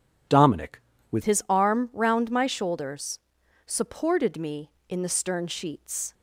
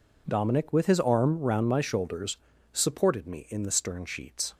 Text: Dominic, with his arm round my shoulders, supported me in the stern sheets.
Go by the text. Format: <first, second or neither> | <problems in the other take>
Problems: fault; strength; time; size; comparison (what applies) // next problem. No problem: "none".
second | changes voice at "his"; from 1.2 s on; 4.9 s long